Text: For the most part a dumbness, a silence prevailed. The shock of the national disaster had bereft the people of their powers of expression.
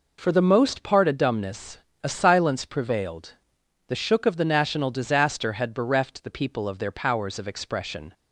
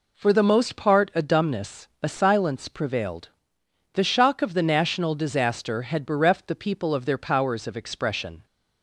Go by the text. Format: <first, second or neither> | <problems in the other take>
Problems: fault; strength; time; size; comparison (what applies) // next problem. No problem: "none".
second | says "shook" for "shock"; at 3.9 s